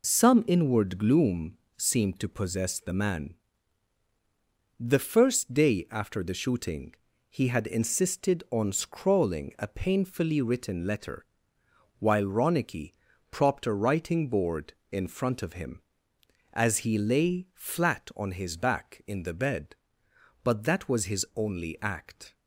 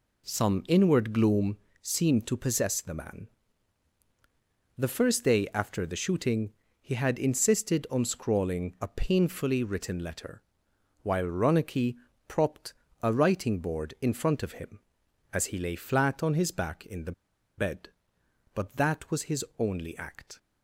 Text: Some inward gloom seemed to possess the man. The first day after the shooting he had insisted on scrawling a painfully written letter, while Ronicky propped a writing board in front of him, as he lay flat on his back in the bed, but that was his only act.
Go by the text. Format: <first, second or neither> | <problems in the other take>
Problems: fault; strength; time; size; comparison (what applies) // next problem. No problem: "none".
first | pauses between "gloom" and "seemed"; slight; at 1.5 s; 0.24 s long; slight in the first // pauses between "shooting" and "he"; slight; at 6.5 s; 0.28 s long; also in the first // pauses between "Ronicky" and "propped"; slight; at 11.9 s; 0.30 s long; also in the first // pauses between "propped" and "a"; slight; at 12.7 s; 0.30 s long // pauses between "the" and "bed"; at 17.1 s; 0.45 s long